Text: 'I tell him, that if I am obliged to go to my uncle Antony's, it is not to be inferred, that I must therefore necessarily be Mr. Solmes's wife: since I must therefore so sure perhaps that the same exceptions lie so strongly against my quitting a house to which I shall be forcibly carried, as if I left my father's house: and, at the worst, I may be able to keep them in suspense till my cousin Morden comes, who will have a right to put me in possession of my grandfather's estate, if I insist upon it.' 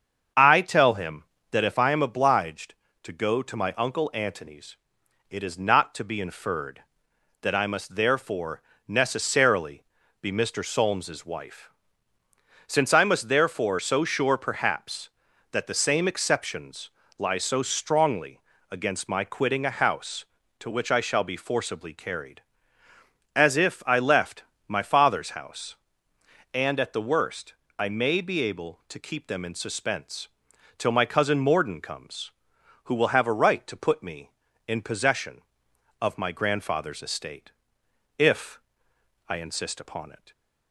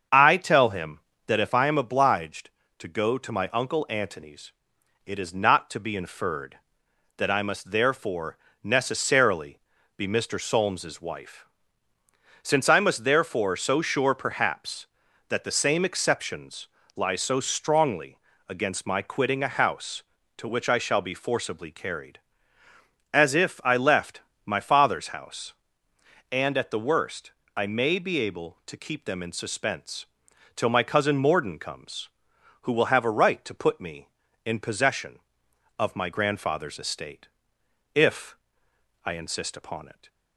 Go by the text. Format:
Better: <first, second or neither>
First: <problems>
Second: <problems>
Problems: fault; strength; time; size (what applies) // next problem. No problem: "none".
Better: neither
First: starts louder than the rest; strong; until 1.6 s; 7 dB // pauses between "therefore" and "necessarily"; slight; at 8.5 s; 0.28 s long // pauses between "necessarily" and "be"; slight; at 9.8 s; 0.36 s long // pauses between "exceptions" and "lie"; slight; at 16.8 s; 0.28 s long // pauses between "strongly" and "against"; slight; at 18.3 s; 0.30 s long // pauses between "left" and "my"; slight; at 24.4 s; 0.26 s long // pauses between "suspense" and "till"; noticeable; at 30.2 s; 0.50 s long // pauses between "if" and "I"; noticeable; at 38.5 s; 0.68 s long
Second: starts louder than the rest; strong; until 1.4 s; 7 dB // pauses between "therefore" and "necessarily"; slight; at 8.3 s; 0.28 s long // pauses between "necessarily" and "be"; slight; at 9.5 s; 0.36 s long // pauses between "exceptions" and "lie"; slight; at 16.6 s; 0.28 s long // pauses between "strongly" and "against"; slight; at 18.1 s; 0.30 s long // pauses between "left" and "my"; slight; at 24.2 s; 0.26 s long // pauses between "suspense" and "till"; noticeable; at 30.0 s; 0.50 s long // pauses between "if" and "I"; noticeable; at 38.3 s; 0.68 s long